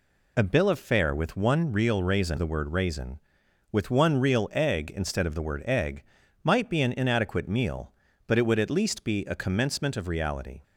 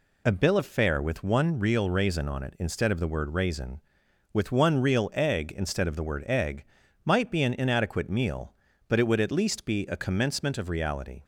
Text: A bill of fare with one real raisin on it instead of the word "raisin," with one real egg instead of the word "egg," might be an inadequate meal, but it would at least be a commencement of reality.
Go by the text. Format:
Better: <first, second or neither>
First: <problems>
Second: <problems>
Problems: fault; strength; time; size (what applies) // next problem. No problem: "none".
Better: second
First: skips "on it instead of"; at 2.3 s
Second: none